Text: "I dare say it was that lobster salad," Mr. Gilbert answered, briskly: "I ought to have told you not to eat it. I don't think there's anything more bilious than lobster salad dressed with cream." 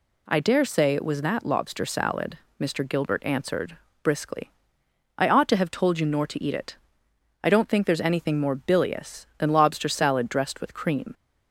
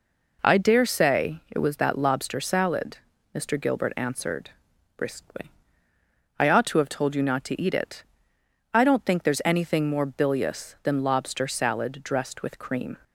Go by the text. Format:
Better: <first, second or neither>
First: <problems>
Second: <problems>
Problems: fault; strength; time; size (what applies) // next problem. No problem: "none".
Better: second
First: says "nor" for "not"; at 6.0 s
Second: none